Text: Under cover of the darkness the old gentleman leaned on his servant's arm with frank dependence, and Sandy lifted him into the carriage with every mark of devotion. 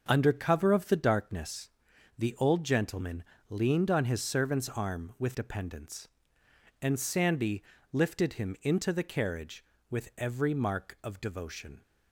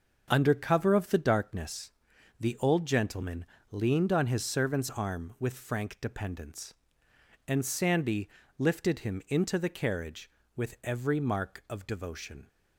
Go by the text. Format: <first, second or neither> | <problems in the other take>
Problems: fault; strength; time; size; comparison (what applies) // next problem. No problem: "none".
second | starts louder than the rest; until 1.0 s; 6.5 dB; also in the second // pauses between "darkness" and "the"; noticeable; at 1.6 s; 0.48 s long; noticeable in the second // pauses between "gentleman" and "leaned"; slight; at 3.2 s; 0.24 s long; slight in the second // skips "frank"; at 5.3 s // pauses between "Sandy" and "lifted"; slight; at 7.6 s; 0.30 s long; slight in the second